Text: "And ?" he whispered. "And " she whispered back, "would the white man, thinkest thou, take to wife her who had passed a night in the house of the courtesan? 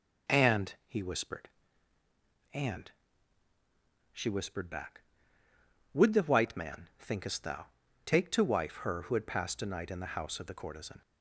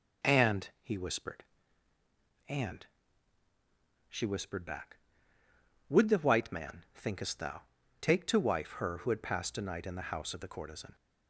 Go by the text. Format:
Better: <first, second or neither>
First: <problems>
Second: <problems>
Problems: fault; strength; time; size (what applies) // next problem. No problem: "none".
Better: neither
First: none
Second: none